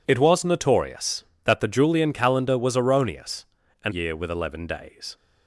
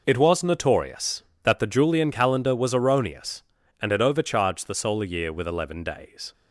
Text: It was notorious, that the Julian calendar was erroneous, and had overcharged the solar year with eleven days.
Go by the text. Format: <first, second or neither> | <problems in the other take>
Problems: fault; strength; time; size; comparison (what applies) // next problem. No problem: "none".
second | skips "had overcharged the solar"; at 3.9 s